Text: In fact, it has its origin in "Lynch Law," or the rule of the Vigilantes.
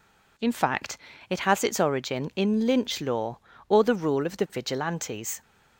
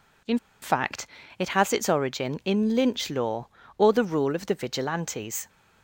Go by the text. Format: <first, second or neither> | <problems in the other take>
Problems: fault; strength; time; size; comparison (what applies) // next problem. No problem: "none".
first | pauses between "In" and "fact"; slight; at 0.3 s; 0.25 s long